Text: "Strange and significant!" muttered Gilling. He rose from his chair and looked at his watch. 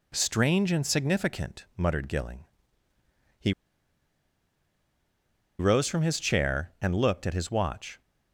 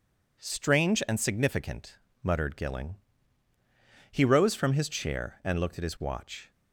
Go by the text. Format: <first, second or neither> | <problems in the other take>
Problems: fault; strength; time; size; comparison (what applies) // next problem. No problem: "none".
second | pauses between "He" and "rose"; strong; at 3.5 s; 2.0 s long